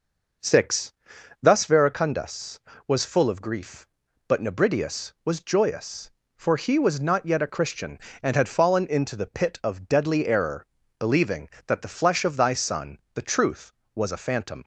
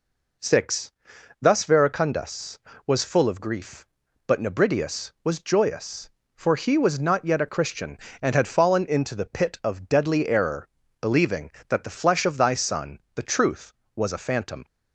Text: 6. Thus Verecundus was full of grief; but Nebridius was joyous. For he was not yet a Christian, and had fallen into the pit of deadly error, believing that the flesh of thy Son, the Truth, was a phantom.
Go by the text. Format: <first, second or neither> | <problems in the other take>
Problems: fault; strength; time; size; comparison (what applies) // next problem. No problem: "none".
second | starts louder than the rest; noticeable; until 1.9 s; 5.5 dB